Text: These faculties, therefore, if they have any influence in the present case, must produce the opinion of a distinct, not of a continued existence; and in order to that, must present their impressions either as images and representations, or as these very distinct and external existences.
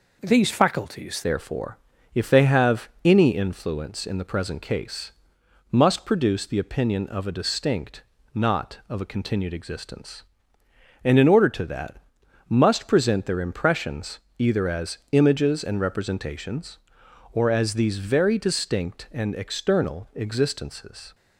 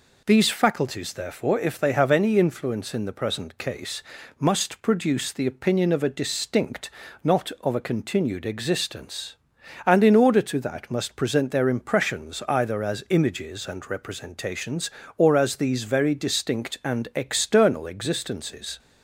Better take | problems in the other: second | changes voice at "therefore"; from 1.2 s on; 19.9 s long // pauses between "impressions" and "either"; slight; at 14.1 s; 0.18 s long

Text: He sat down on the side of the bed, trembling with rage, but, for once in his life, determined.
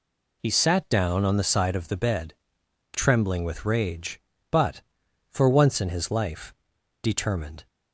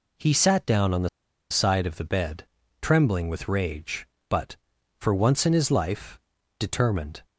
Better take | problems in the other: first | pauses between "the" and "side"; at 1.0 s; 0.42 s long

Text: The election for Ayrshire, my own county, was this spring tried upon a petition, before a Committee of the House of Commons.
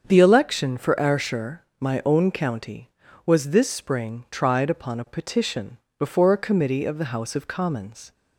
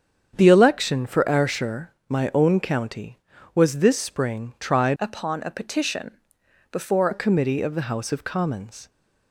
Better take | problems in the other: first | starts louder than the rest; strong; until 1.4 s; 8 dB; strong in the first // changes voice from "upon" to "before"; from 4.9 to 7.0 s; 2.1 s long

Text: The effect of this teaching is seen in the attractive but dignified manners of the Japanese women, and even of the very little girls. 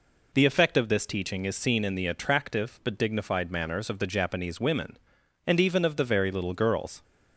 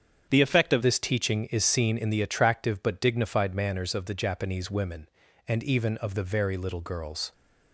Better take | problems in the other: first | starts louder than the rest; strong; until 1.3 s; 8 dB // changes voice at "this"; from 0.8 s on; 6.5 s long

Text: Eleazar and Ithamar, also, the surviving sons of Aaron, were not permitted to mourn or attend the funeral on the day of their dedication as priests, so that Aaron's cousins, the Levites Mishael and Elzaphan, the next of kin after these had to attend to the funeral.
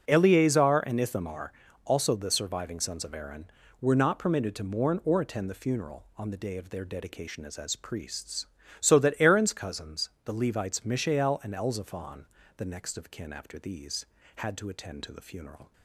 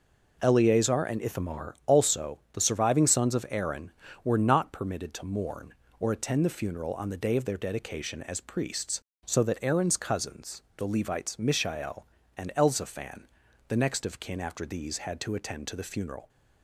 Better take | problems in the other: second | starts louder than the rest; strong; until 1.0 s; 7 dB // says "as" twice; at 7.5 s

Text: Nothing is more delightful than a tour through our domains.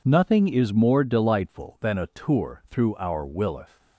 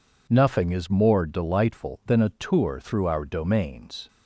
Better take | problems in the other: second | says "willeth" for "domains"; at 3.2 s

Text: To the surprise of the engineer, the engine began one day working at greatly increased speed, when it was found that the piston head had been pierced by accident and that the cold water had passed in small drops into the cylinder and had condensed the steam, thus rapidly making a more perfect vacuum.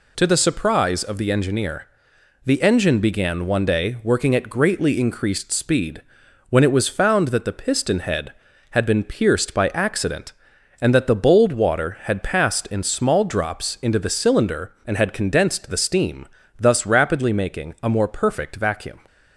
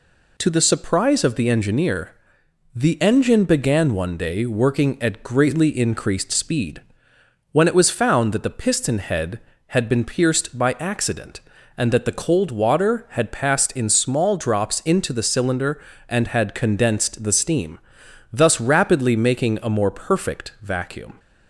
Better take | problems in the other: second | says "bold" for "cold"; at 11.1 s

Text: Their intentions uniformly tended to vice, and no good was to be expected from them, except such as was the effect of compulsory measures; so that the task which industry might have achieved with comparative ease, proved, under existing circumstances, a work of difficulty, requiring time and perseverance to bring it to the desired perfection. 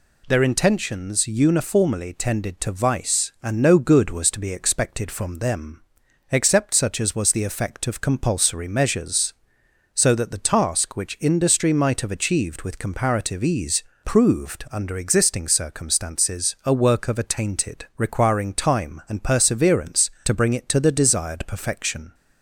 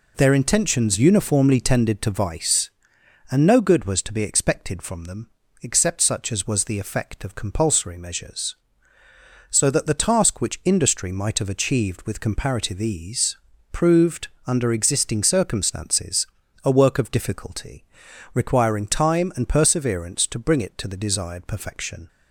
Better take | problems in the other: second | says "attainted" for "difficulty"; at 17.1 s

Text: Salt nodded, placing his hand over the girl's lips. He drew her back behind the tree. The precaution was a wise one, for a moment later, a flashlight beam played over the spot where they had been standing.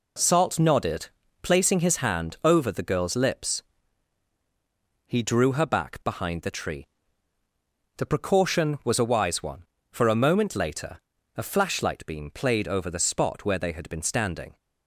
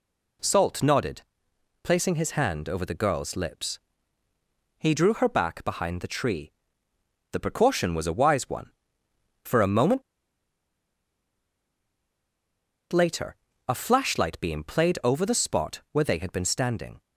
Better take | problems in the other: first | pauses between "moment" and "later"; strong; at 10.0 s; 2.9 s long

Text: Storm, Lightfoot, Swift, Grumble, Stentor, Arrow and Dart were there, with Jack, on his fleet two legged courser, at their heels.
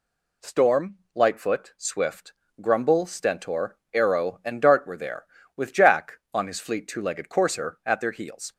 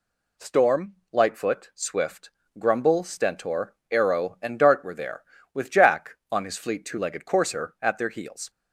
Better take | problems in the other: neither | none

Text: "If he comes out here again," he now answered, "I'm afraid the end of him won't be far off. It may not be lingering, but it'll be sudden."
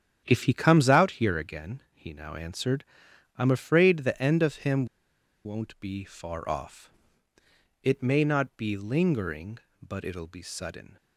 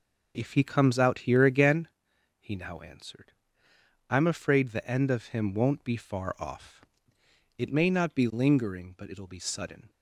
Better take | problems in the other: second | starts louder than the rest; strong; until 1.2 s; 9.5 dB // pauses between "him" and "won't"; noticeable; at 4.8 s; 0.59 s long

